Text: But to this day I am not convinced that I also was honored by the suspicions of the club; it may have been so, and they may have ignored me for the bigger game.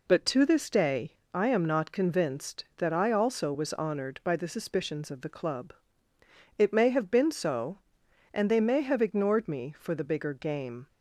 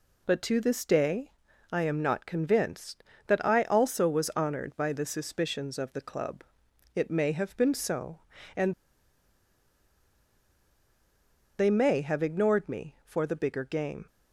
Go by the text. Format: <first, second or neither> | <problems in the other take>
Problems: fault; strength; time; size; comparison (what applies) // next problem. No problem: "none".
first | pauses between "day" and "I"; at 1.3 s; 0.40 s long; slight in the first // pauses between "and" and "they"; strong; at 8.7 s; 2.8 s long